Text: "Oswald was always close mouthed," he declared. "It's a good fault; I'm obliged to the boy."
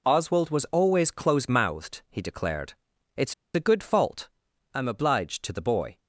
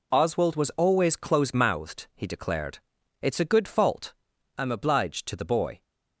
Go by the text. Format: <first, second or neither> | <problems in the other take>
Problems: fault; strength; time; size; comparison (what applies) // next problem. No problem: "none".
second | pauses between "It's" and "a"; slight; at 3.3 s; 0.20 s long